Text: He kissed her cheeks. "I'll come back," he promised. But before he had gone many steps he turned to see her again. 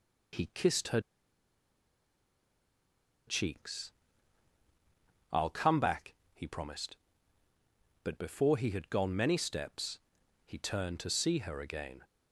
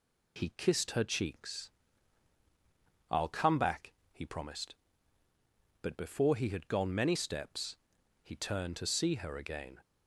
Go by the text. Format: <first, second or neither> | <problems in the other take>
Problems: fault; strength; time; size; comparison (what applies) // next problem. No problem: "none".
second | pauses between "her" and "cheeks"; strong; at 0.9 s; 2.2 s long // pauses between "steps" and "he"; at 10.0 s; 0.44 s long; also in the second